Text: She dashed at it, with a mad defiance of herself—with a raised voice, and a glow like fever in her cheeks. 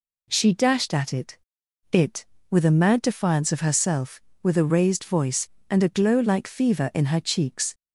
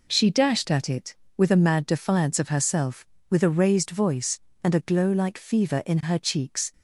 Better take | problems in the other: second | says "it" twice; at 1.9 s

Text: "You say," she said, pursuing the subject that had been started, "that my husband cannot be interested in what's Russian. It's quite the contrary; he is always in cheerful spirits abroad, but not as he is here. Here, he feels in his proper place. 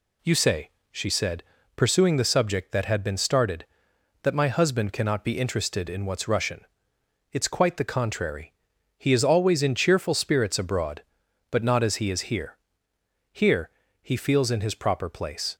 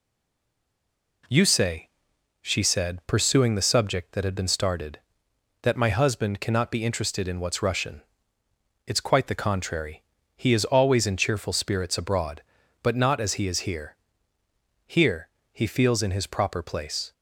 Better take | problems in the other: first | stays silent before the first word; noticeable; until 1.2 s; 1.2 s long

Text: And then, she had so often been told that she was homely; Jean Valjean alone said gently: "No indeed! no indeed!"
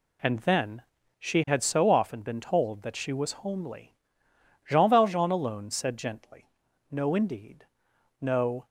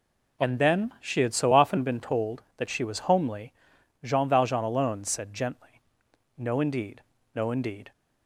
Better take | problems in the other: second | stops before "indeed"; at 8.6 s

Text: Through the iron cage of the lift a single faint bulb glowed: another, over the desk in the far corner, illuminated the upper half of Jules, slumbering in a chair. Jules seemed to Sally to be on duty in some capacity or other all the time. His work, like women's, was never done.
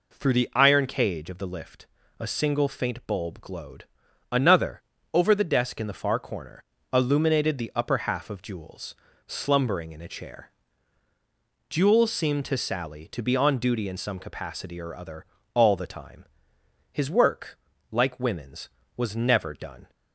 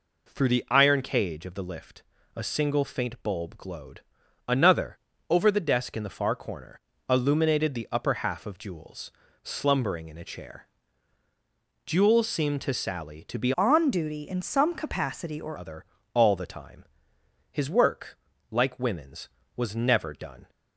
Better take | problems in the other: first | pauses between "lift" and "a"; slight; at 2.0 s; 0.32 s long; slight in the first // changes voice from "on" to "or"; from 13.5 to 15.5 s; 2.0 s long // pauses between "other" and "all"; slight; at 15.8 s; 0.30 s long; slight in the first

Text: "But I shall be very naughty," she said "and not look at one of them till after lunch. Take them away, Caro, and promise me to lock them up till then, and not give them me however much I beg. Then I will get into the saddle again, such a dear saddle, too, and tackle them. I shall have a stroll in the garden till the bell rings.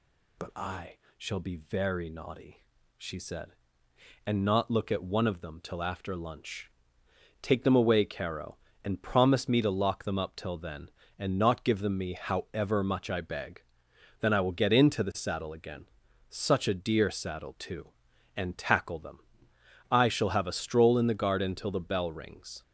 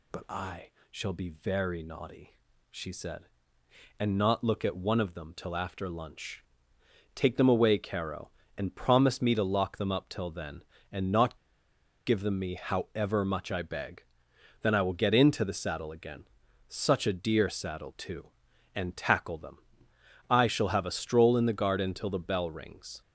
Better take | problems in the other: first | pauses between "I" and "shall"; slight; at 0.6 s; 0.22 s long; slight in the first // pauses between "not" and "give"; noticeable; at 11.3 s; 0.69 s long

